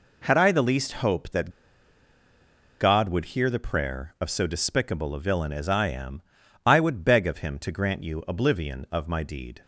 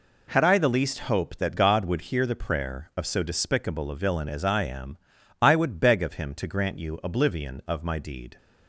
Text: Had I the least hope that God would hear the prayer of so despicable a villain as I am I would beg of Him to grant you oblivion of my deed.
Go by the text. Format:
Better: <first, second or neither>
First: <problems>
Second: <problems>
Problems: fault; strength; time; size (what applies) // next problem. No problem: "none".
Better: second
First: pauses between "that" and "God"; strong; at 1.5 s; 1.3 s long // pauses between "am" and "I"; at 6.2 s; 0.44 s long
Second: pauses between "am" and "I"; at 4.9 s; 0.44 s long